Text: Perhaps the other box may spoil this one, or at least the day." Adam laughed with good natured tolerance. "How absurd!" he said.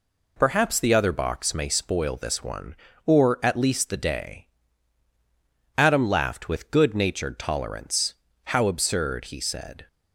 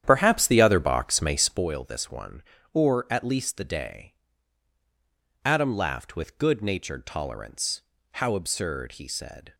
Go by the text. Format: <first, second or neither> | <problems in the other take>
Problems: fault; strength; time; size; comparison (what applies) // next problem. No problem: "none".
first | starts louder than the rest; strong; until 1.7 s; 10 dB